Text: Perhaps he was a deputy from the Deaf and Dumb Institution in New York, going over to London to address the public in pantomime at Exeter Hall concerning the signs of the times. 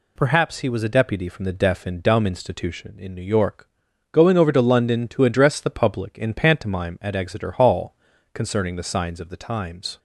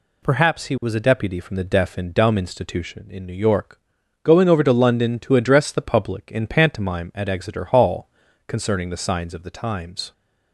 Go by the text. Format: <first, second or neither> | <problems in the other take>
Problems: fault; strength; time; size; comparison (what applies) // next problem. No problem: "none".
neither | pauses between "Hall" and "concerning"; slight; the same in both